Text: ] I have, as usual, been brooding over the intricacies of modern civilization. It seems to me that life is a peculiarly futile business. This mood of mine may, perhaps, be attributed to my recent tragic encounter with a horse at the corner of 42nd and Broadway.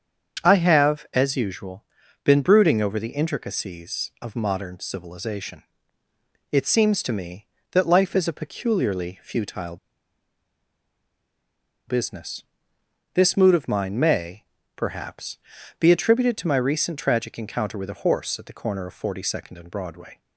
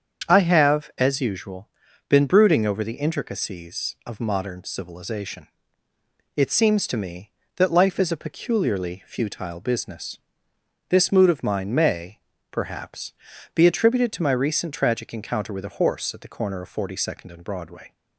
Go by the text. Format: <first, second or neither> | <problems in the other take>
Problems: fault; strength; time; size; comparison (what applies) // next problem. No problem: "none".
second | starts louder than the rest; strong; until 1.5 s; 7.5 dB; strong in the second // pauses between "futile" and "business"; strong; at 9.7 s; 2.1 s long